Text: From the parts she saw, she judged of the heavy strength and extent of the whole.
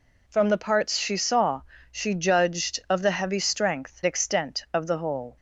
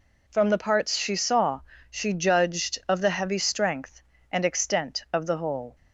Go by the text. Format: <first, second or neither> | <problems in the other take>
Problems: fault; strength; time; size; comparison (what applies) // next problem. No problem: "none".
second | skips "and"; at 4.0 s